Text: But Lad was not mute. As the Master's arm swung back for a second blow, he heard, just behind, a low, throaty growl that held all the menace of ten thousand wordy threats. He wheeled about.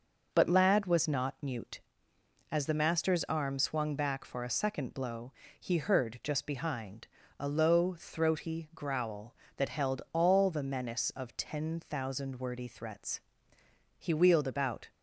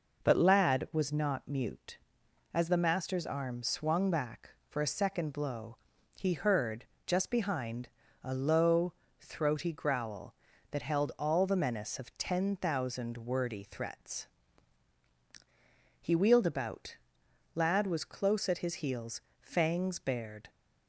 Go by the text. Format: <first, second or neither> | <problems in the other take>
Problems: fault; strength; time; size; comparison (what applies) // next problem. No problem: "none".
first | goes on to say "Lad was close at his heels fangs bared"; strong; from 17.5 s on; 2.9 s long